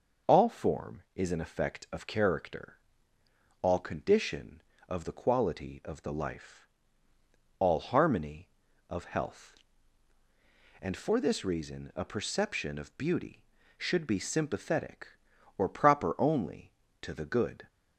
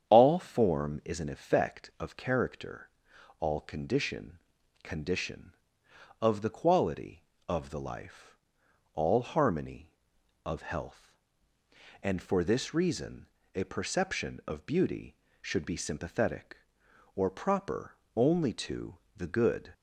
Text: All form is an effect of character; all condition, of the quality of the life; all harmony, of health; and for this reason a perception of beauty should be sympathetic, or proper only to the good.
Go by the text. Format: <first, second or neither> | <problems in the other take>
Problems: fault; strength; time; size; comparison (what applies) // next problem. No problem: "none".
first | starts louder than the rest; strong; until 1.1 s; 8.5 dB // says "condition" twice; at 4.8 s // pauses between "reason" and "a"; slight; at 13.2 s; 0.26 s long // pauses between "proper" and "only"; slight; at 17.9 s; 0.18 s long // pauses between "to" and "the"; slight; at 18.9 s; 0.18 s long